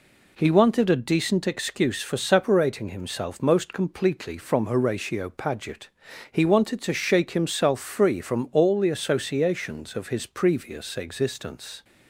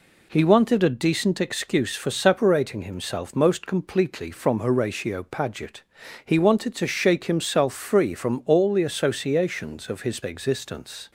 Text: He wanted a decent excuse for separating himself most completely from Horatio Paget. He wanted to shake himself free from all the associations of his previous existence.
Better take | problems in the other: first | skips "previous"; at 10.2 s

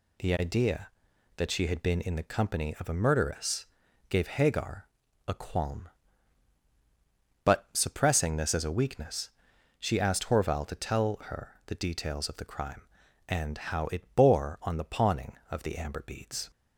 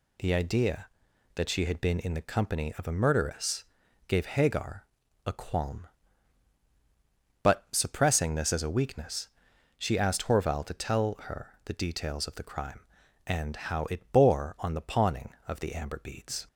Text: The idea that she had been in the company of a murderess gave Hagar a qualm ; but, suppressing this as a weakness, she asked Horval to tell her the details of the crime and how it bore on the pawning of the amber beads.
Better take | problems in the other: neither | pauses between "murderess" and "gave"; the same in both // pauses between "Hagar" and "a"; the same in both

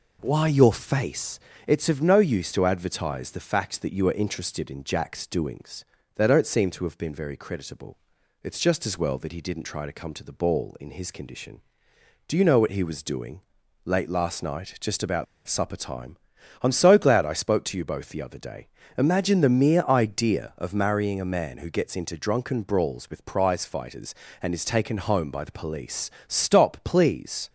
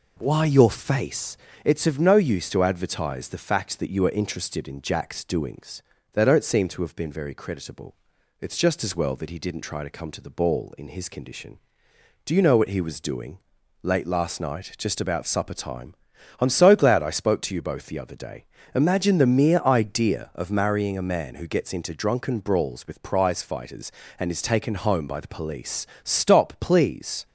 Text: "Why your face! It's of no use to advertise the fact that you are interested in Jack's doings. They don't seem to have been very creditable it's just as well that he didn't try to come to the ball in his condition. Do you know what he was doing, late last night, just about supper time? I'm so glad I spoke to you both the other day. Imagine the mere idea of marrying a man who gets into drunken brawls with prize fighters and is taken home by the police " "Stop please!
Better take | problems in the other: second | pauses between "creditable" and "it's"; noticeable; at 7.9 s; 0.46 s long; noticeable in the second // pauses between "about" and "supper"; slight; at 15.2 s; 0.21 s long

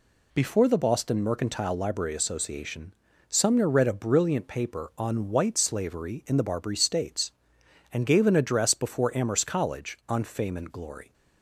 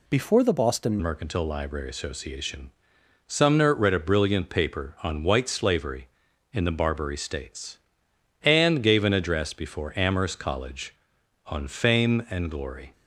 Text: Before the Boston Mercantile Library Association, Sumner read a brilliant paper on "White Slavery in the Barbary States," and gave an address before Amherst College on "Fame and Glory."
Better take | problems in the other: first | changes voice at "Mercantile"; from 1.0 s on; 11.9 s long

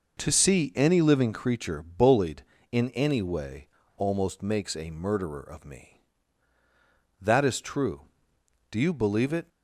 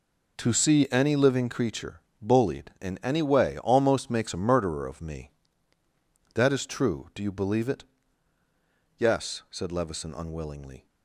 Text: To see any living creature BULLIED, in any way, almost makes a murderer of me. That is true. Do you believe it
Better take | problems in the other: first | pauses between "creature" and "BULLIED"; slight; at 2.0 s; 0.20 s long // goes on to say "Yes said Levison unwillingly"; strong; from 8.9 s on; 1.8 s long

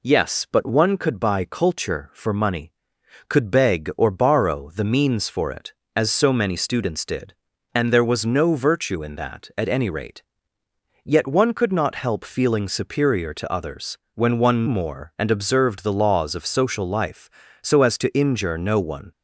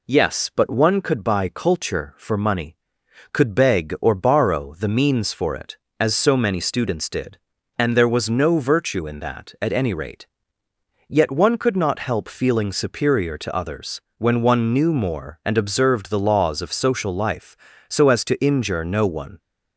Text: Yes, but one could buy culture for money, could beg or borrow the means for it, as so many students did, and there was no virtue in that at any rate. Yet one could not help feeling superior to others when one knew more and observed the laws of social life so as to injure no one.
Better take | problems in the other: second | pauses between "others" and "when"; slight; at 13.9 s; 0.16 s long; slight in the second // skips "knew"; at 14.6 s

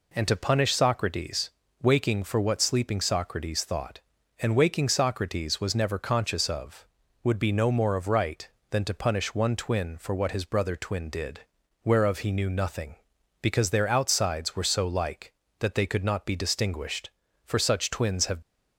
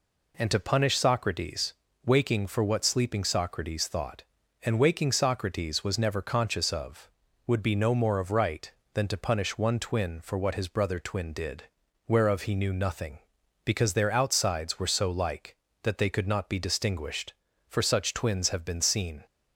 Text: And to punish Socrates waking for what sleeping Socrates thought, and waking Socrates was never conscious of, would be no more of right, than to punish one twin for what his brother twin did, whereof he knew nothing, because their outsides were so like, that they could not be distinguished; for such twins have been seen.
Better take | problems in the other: second | pauses between "Socrates" and "waking"; slight; at 1.5 s; 0.32 s long; slight in the second // stops before "been seen"; at 18.4 s

